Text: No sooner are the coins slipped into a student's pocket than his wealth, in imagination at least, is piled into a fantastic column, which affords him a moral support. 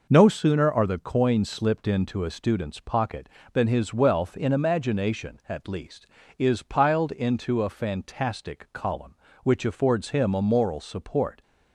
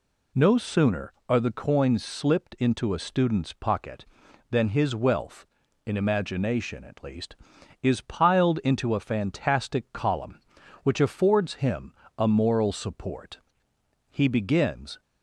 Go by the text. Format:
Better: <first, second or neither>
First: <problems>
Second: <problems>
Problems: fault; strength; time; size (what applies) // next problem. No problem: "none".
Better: first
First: none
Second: pauses between "him" and "a"; slight; at 11.9 s; 0.24 s long // goes on to say "He begins"; noticeable; from 14.0 s on; 0.92 s long